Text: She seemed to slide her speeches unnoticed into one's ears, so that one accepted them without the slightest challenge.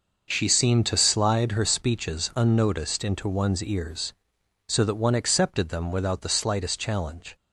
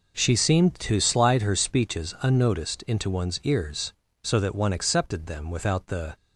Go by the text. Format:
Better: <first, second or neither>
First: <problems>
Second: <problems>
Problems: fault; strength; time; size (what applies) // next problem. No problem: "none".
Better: first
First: none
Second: stops before "slightest challenge"; at 6.1 s